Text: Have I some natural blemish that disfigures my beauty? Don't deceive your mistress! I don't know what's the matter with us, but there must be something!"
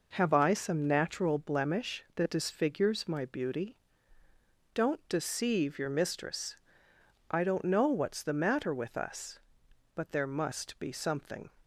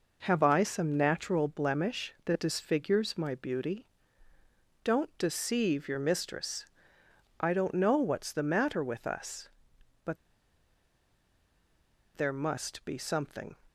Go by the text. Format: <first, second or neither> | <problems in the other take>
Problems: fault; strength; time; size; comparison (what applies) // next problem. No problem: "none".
first | pauses between "but" and "there"; strong; at 10.1 s; 1.9 s long